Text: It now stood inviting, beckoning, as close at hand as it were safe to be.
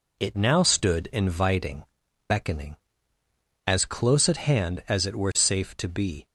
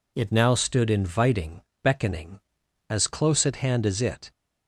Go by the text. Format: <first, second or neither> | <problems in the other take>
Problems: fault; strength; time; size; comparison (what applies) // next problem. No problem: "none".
first | stops before "were safe to be"; at 4.3 s